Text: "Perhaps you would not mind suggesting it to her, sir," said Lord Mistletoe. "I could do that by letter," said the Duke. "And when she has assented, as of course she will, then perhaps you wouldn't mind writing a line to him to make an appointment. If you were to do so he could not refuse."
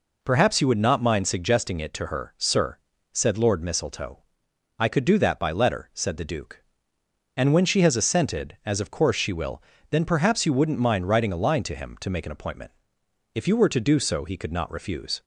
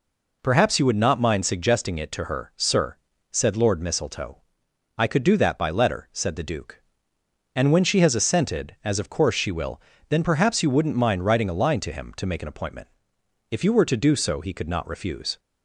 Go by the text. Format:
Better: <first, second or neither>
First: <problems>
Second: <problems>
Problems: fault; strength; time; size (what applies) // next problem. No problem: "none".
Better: neither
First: none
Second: none